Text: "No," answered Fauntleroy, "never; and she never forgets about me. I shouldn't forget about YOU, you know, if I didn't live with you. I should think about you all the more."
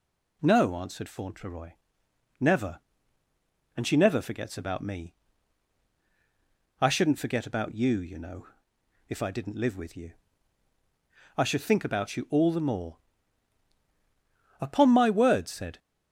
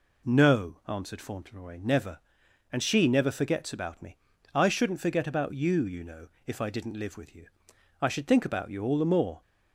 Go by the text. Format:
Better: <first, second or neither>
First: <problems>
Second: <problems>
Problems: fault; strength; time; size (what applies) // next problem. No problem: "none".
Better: second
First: goes on to say "Upon my word said"; noticeable; from 14.6 s on; 1.1 s long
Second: none